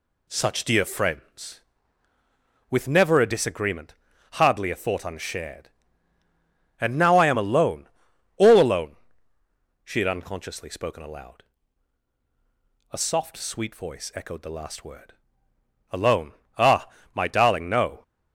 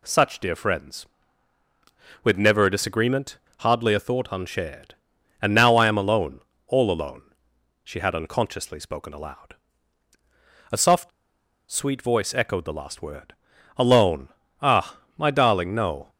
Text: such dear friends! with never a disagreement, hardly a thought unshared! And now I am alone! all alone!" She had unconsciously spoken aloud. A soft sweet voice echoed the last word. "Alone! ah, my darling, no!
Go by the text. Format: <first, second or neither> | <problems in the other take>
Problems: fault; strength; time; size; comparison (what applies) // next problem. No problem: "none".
first | pauses between "soft" and "sweet"; noticeable; at 11.1 s; 0.60 s long